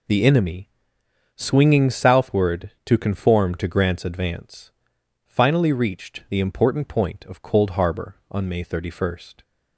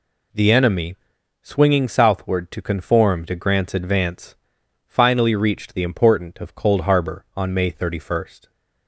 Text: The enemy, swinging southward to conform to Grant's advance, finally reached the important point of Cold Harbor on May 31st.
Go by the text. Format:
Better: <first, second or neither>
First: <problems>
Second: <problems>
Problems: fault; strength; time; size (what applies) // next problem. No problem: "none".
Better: first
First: none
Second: skips "point"; at 6.3 s